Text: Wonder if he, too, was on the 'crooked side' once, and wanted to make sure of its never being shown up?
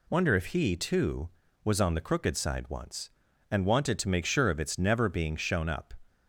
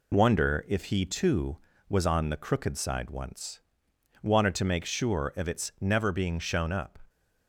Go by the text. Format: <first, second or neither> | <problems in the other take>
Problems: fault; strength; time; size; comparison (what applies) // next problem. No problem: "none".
first | skips "and"; at 3.9 s